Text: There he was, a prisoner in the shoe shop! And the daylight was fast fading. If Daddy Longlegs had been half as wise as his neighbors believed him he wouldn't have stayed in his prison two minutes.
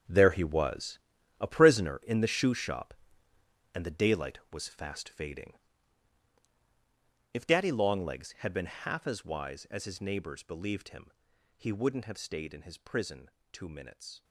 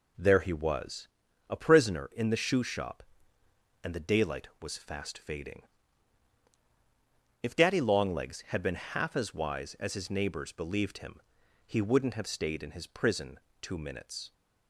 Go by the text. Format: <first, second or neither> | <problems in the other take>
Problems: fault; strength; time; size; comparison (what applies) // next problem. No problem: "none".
second | gets quieter; strong; throughout; 13.5 dB // pauses between "him" and "he"; noticeable; at 11.0 s; 0.46 s long; noticeable in the second // pauses between "prison" and "two"; slight; at 13.2 s; 0.22 s long; slight in the second